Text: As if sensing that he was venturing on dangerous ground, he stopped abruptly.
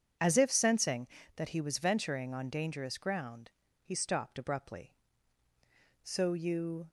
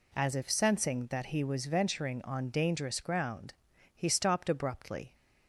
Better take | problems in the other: second | goes on to say "So you"; noticeable; from 6.0 s on; 0.86 s long

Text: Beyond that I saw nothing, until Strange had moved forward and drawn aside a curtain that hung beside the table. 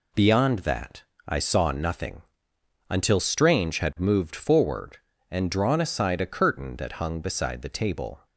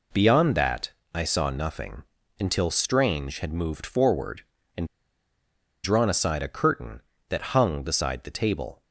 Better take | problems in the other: first | pauses between "that" and "I"; slight; at 0.9 s; 0.22 s long; slight in the first // pauses between "and" and "drawn"; at 4.8 s; 0.98 s long

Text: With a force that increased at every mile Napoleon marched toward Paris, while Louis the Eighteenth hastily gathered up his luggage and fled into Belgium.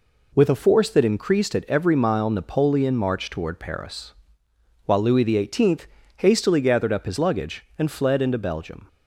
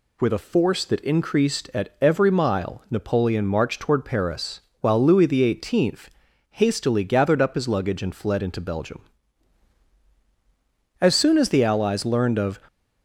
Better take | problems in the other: first | pauses between "Eighteenth" and "hastily"; at 6.0 s; 0.42 s long; slight in the first // goes on to say "As soon as the Allies learned of"; from 10.9 s on; 1.6 s long

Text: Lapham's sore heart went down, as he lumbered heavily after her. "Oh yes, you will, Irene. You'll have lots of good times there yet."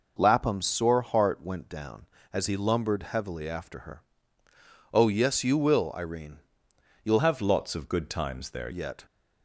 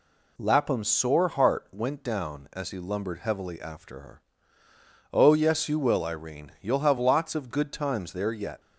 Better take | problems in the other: second | changes voice from "have" to "there"; from 7.1 to 8.7 s; 1.6 s long

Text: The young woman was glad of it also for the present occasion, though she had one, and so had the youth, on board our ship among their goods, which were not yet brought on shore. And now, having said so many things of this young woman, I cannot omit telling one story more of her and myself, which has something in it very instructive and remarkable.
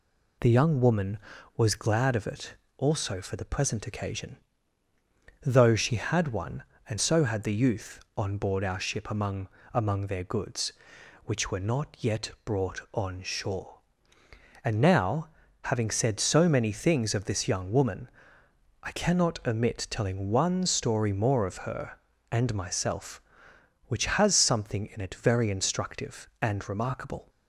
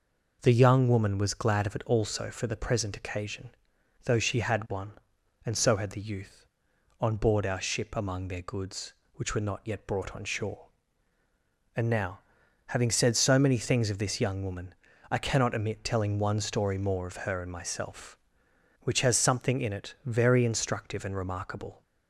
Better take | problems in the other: second | pauses between "it" and "also"; slight; at 2.5 s; 0.22 s long // says "among" twice; at 9.7 s

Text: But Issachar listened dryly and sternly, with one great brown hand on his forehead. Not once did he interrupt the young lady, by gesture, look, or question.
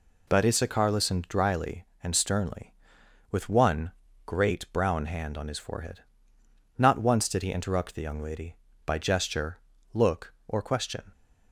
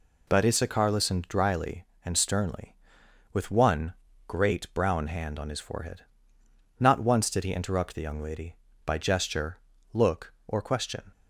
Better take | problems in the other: neither | pauses between "one" and "great"; slight; the same in both

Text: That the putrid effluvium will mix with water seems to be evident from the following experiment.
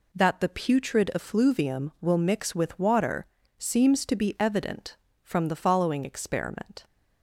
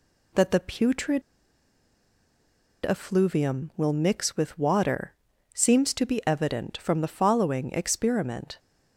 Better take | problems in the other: first | pauses between "putrid" and "effluvium"; strong; at 1.2 s; 1.6 s long // pauses between "water" and "seems"; at 5.1 s; 0.42 s long; slight in the first

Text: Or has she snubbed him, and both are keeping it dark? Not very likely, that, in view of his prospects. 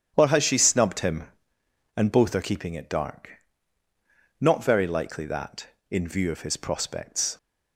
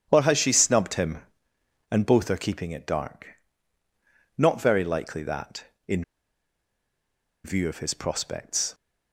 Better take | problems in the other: first | starts louder than the rest; strong; until 1.1 s; 9.5 dB; strong in the first // pauses between "in" and "view"; strong; at 6.0 s; 1.4 s long

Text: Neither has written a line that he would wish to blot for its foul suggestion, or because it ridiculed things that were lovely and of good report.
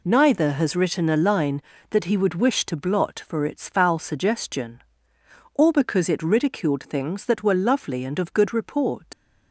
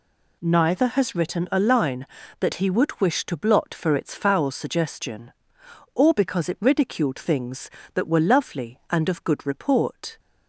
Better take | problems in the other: second | leaves "report" unfinished; at 9.1 s; 90 ms

